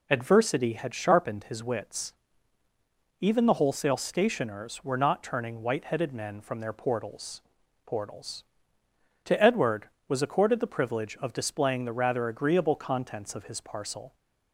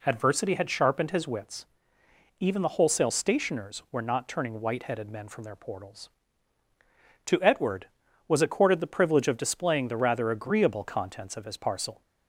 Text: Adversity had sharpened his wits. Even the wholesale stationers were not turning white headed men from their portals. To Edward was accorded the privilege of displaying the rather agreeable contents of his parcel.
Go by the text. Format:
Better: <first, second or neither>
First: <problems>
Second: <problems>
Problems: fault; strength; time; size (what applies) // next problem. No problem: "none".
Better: second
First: says "portals" twice; at 7.8 s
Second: none